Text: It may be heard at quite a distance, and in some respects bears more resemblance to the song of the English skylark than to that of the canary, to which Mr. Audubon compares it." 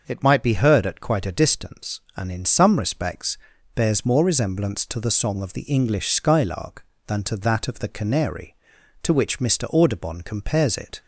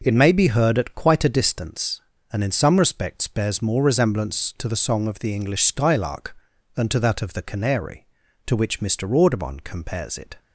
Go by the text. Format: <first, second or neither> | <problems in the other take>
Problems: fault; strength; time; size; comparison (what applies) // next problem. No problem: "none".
second | starts louder than the rest; noticeable; until 1.0 s; 6 dB // says "might" for "may"; at 0.2 s // pauses between "respects" and "bears"; at 3.3 s; 0.38 s long